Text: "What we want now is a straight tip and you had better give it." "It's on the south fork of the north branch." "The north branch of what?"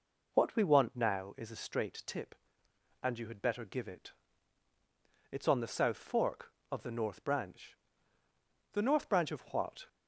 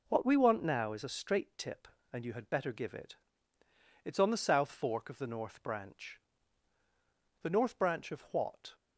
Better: neither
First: none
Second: none

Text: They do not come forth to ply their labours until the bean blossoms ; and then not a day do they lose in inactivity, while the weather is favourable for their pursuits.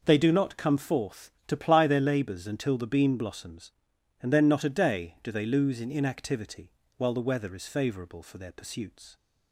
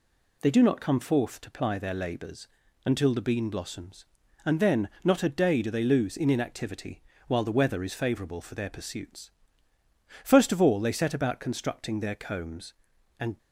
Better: first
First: none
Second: pauses between "labours" and "until"; at 2.4 s; 0.38 s long // pauses between "then" and "not"; slight; at 4.8 s; 0.16 s long // goes on to say "First of all they set about constructing their combs and"; strong; from 10.2 s on; 3.1 s long

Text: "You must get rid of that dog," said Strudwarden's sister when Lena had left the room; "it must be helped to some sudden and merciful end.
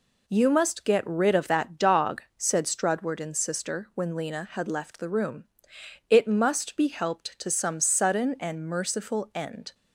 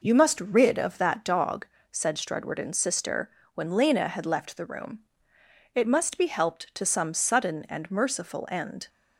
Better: first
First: none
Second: skips "get"; at 0.4 s // pauses between "sister" and "when"; slight; at 3.3 s; 0.24 s long

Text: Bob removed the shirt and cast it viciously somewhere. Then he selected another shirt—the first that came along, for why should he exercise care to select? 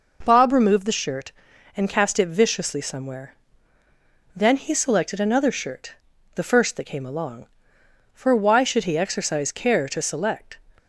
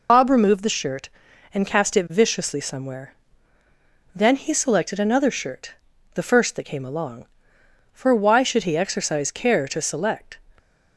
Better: first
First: none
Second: loses the start of "Bob"; at 0.0 s; 125 ms

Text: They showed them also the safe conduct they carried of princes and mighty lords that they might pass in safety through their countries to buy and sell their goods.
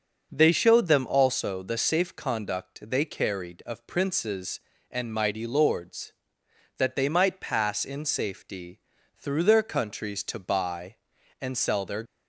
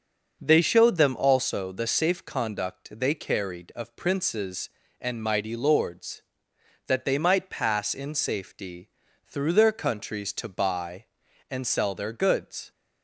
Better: second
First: starts louder than the rest; until 1.3 s; 6.5 dB // pauses between "safety" and "through"; at 8.7 s; 0.38 s long // stops before "goods"; at 12.0 s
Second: starts louder than the rest; until 1.4 s; 6.5 dB // pauses between "safety" and "through"; at 8.8 s; 0.38 s long

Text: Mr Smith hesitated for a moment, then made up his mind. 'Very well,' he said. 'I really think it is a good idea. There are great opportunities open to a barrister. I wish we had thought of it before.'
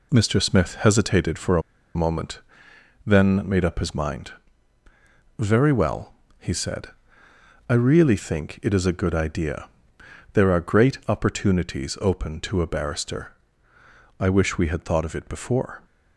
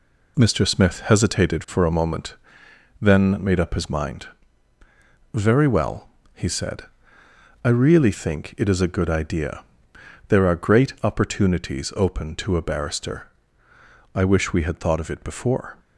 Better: second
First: pauses between "a" and "moment"; slight; at 1.6 s; 0.35 s long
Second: none

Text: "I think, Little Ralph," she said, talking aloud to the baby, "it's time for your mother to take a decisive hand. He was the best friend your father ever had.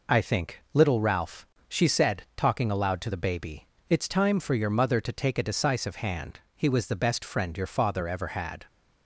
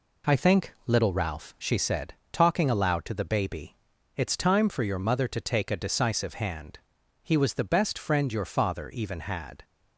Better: first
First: none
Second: says "even" for "ever"; at 8.8 s

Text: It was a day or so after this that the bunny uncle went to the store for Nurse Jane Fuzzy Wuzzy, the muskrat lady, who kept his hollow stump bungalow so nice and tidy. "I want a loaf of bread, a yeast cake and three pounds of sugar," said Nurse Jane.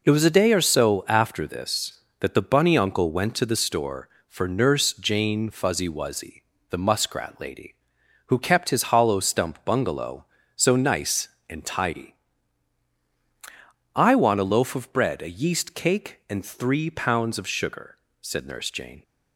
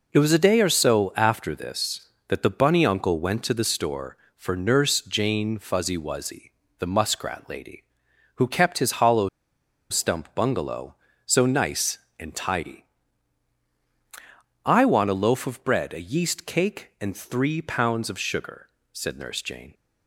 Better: first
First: none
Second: pauses between "hollow" and "stump"; noticeable; at 9.2 s; 0.61 s long

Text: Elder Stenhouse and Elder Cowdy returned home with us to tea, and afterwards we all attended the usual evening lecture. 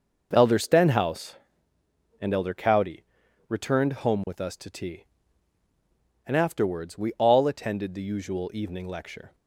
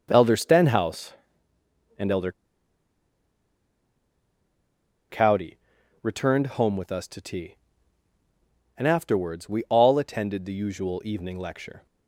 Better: first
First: pauses between "Cowdy" and "returned"; noticeable; at 3.0 s; 0.46 s long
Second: pauses between "Elder" and "Cowdy"; strong; at 2.3 s; 2.7 s long // pauses between "Cowdy" and "returned"; noticeable; at 5.5 s; 0.46 s long

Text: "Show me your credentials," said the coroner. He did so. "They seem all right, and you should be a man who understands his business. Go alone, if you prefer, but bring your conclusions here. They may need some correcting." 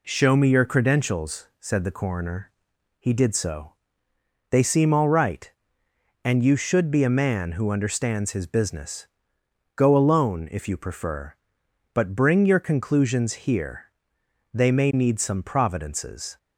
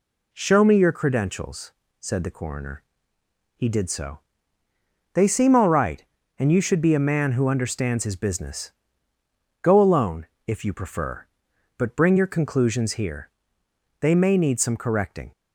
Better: second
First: says "providences" for "correcting"; at 15.4 s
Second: none

